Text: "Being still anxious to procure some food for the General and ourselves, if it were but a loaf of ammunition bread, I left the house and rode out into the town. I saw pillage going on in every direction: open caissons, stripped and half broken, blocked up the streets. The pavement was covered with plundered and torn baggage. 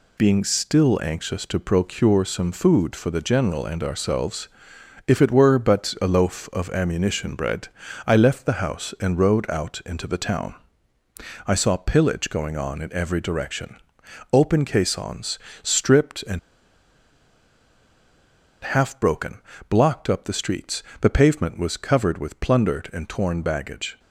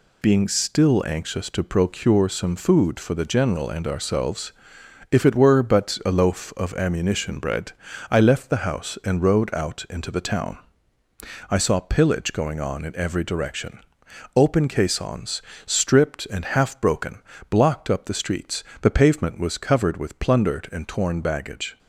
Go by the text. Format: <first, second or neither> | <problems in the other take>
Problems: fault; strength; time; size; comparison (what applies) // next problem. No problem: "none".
second | pauses between "and" and "half"; strong; at 16.3 s; 2.2 s long